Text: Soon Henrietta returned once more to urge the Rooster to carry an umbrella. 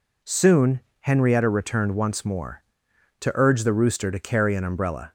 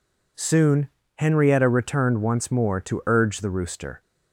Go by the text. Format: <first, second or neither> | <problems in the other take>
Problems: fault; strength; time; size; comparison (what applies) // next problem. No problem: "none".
first | pauses between "Soon" and "Henrietta"; slight; at 0.8 s; 0.28 s long; slight in the first // stops before "to carry an umbrella"; at 4.0 s